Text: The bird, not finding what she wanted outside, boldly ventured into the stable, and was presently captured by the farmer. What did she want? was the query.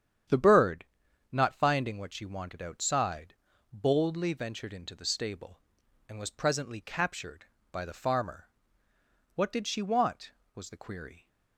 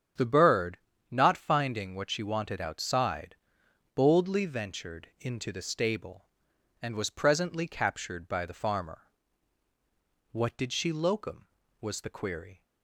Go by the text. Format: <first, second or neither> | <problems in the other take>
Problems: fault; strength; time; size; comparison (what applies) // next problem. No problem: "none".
first | starts louder than the rest; strong; until 1.4 s; 8 dB; strong in the first // says "locum" for "want"; at 10.9 s